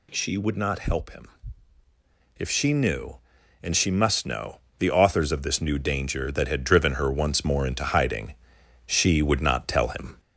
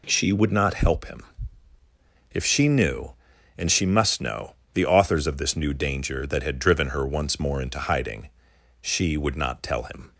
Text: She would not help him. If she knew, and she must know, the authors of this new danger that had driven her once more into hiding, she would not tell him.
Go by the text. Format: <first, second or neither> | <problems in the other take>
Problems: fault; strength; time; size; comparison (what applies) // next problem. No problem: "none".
second | gets louder; slight; throughout; 2 dB